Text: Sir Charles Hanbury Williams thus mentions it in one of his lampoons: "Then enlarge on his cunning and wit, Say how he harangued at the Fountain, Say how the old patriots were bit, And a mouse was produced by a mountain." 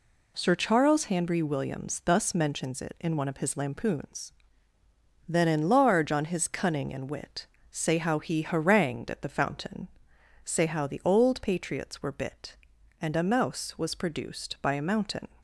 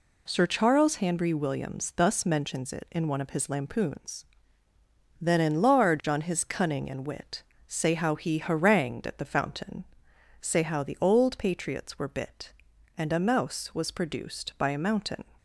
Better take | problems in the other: neither | none

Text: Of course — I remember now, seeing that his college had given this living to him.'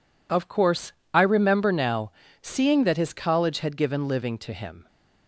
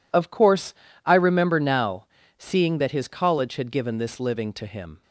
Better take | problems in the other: second | skips "this"; at 4.0 s

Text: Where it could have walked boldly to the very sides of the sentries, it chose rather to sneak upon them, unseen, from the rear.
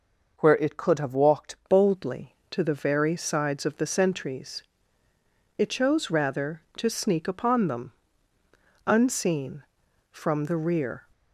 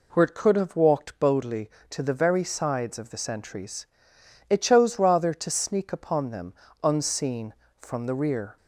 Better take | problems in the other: second | changes voice at "boldly"; from 1.6 s on; 9.4 s long

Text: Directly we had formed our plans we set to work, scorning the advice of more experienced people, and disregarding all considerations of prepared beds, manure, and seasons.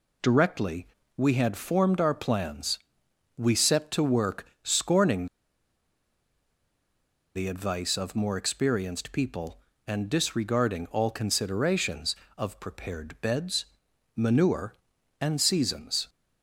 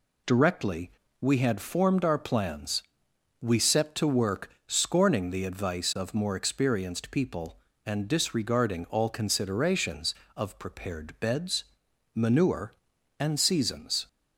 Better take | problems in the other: second | pauses between "Directly" and "we"; slight; at 0.8 s; 0.30 s long; slight in the second // pauses between "plans" and "we"; noticeable; at 2.7 s; 0.60 s long; noticeable in the second // pauses between "scorning" and "the"; strong; at 5.2 s; 2.0 s long

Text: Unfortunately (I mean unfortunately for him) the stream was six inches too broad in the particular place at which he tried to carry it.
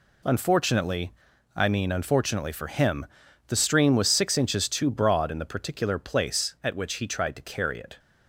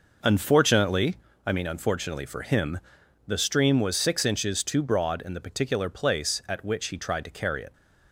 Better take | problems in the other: neither | none

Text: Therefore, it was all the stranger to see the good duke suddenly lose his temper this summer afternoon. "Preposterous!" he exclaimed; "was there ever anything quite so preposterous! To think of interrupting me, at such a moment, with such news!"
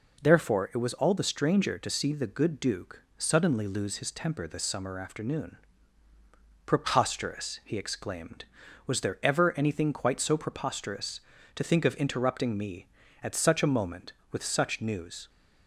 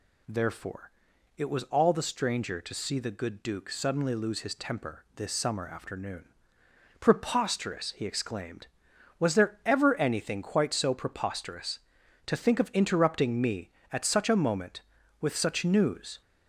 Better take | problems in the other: neither | none

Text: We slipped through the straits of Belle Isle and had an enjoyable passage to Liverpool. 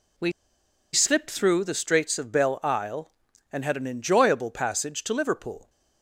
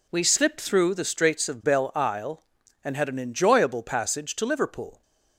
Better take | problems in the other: second | pauses between "We" and "slipped"; noticeable; at 0.3 s; 0.61 s long

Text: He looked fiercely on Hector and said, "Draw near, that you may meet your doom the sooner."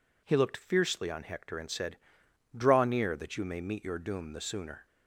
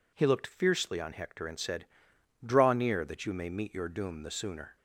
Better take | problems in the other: neither | none

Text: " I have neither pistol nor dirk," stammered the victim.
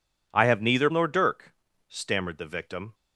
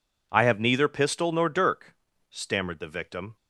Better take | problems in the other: second | skips "pistol"; at 0.8 s

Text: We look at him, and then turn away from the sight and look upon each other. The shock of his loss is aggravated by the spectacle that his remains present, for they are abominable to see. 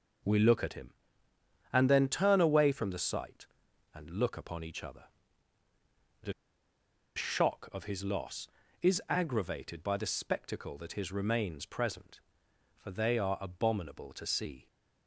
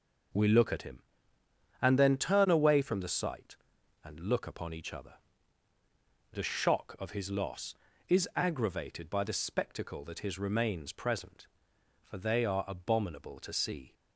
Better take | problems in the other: second | pauses between "The" and "shock"; noticeable; at 6.3 s; 0.83 s long

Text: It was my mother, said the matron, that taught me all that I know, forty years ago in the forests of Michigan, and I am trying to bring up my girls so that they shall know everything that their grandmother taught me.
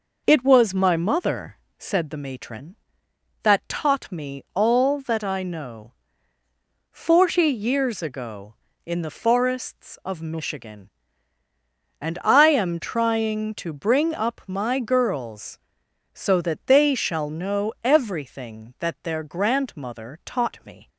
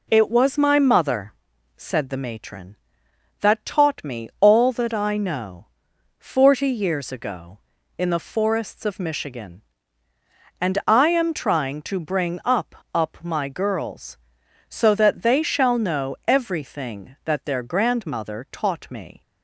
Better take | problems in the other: first | says "up" twice; at 12.9 s

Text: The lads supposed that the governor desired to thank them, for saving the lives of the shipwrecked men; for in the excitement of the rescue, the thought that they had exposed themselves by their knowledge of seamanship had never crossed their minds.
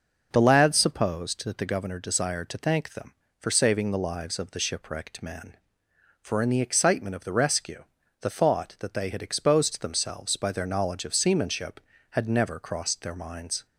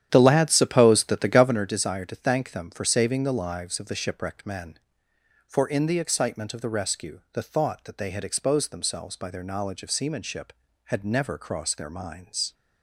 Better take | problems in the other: first | starts louder than the rest; strong; until 1.7 s; 10 dB

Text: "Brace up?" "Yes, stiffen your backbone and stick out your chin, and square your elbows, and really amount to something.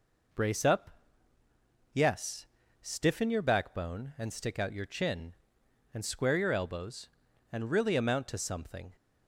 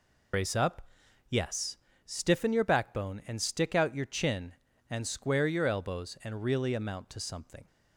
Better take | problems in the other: first | loses the start of "Brace"; at 0.3 s; 65 ms

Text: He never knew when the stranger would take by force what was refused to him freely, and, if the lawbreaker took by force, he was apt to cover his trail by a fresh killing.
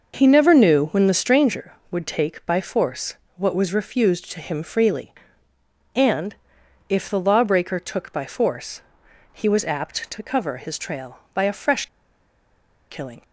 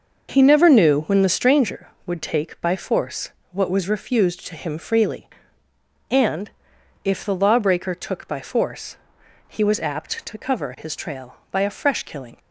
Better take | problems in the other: second | pauses between "force" and "what"; slight; at 3.1 s; 0.20 s long; slight in the second // pauses between "fresh" and "killing"; at 11.8 s; 1.0 s long

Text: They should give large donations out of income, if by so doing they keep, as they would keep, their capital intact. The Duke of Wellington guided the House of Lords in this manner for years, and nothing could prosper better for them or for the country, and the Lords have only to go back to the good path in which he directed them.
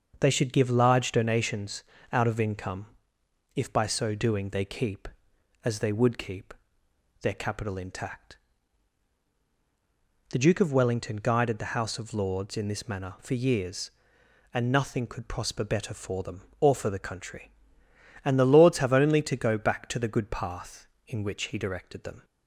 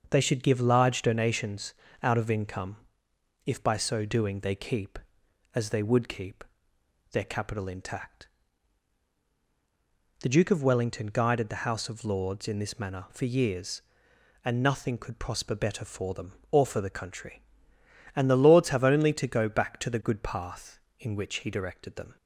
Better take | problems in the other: neither | starts louder than the rest; noticeable; the same in both // pauses between "donations" and "out"; slight; the same in both

